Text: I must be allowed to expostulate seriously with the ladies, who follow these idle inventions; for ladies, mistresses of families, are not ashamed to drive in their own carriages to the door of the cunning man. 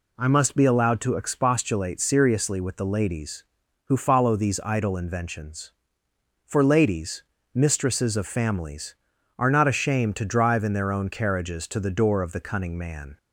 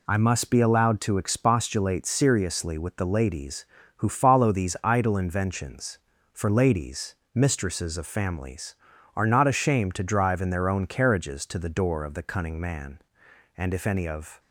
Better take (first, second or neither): first